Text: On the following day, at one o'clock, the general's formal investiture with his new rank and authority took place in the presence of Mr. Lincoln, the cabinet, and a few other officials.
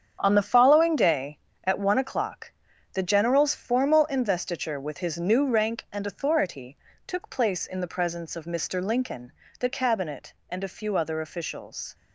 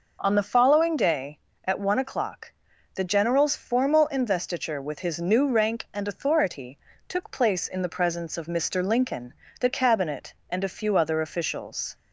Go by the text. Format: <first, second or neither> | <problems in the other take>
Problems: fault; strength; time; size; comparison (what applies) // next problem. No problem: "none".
second | gets quieter; strong; throughout; 9.5 dB // pauses between "authority" and "took"; slight; at 6.7 s; 0.30 s long; slight in the second